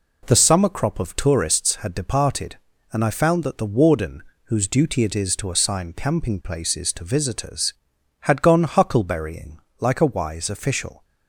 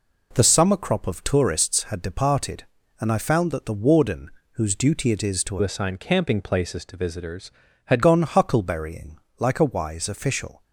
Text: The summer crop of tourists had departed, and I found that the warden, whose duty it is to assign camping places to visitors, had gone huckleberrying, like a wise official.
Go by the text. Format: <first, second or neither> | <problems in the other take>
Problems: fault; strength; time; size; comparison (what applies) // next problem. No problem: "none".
first | changes voice from "assign" to "had"; from 5.6 to 8.0 s; 2.4 s long